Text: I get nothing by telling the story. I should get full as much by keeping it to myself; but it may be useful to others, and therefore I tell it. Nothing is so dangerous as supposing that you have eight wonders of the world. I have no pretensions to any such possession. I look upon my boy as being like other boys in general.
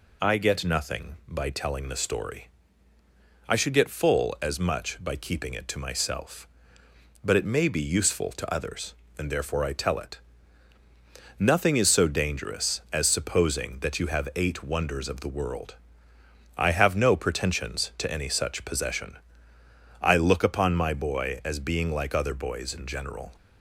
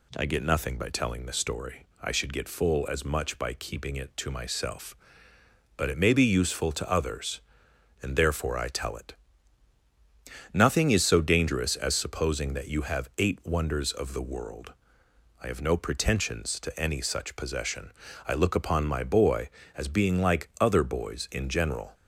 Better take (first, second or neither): neither